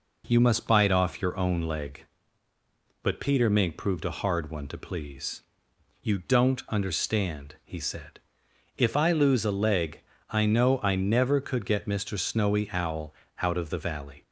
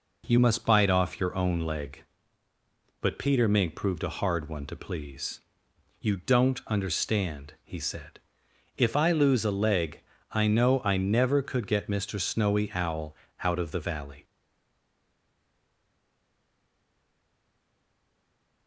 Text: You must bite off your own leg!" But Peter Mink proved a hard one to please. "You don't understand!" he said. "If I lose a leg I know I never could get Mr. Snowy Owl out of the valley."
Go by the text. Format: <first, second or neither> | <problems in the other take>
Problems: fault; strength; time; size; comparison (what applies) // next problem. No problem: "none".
first | pauses between "leg" and "I"; slight; at 9.9 s; 0.32 s long; slight in the first // pauses between "Owl" and "out"; slight; at 13.1 s; 0.30 s long; slight in the first // stays silent after the last word; strong; from 14.2 s on; 4.4 s long